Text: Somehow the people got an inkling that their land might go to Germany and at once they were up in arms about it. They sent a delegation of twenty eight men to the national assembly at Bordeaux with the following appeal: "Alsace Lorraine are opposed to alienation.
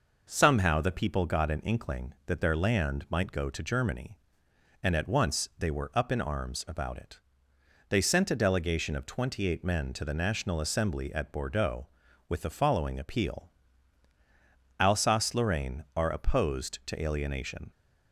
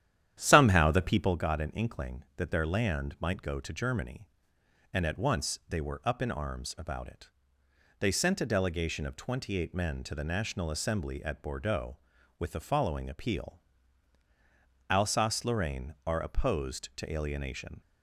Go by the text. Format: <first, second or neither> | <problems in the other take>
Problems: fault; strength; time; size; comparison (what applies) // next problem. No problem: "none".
first | starts louder than the rest; strong; until 1.4 s; 10.5 dB